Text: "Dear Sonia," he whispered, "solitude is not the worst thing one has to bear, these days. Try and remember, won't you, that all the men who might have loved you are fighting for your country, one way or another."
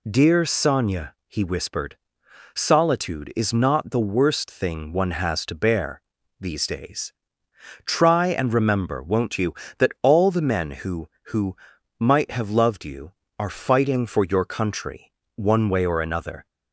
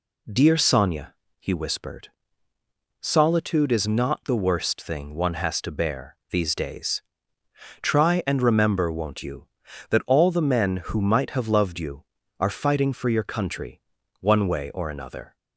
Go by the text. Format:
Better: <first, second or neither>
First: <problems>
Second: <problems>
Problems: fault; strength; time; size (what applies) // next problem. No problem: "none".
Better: second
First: says "who" twice; at 11.3 s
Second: none